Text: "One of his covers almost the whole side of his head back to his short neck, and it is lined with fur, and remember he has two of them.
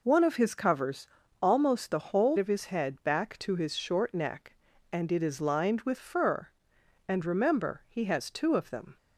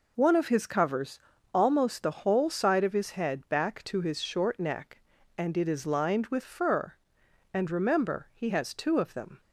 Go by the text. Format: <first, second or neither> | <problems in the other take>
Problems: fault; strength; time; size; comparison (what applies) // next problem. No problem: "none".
second | pauses between "covers" and "almost"; slight; at 1.0 s; 0.32 s long; slight in the second // skips "side"; at 2.3 s